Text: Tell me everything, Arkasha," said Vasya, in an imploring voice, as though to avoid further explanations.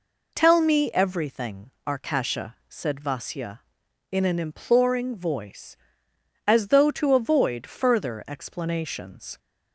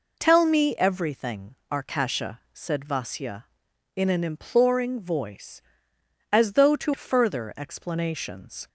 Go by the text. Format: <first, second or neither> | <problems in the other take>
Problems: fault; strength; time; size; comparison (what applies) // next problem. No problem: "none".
first | skips "avoid"; at 6.9 s